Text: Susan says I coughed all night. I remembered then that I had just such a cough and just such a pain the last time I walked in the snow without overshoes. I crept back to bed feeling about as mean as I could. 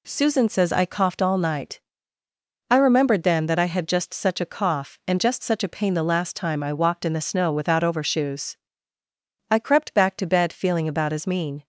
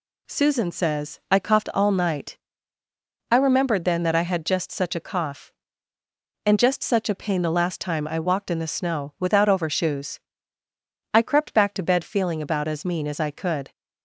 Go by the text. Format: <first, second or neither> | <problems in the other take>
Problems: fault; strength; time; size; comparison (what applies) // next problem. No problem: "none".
second | stops before "as I could"; at 11.6 s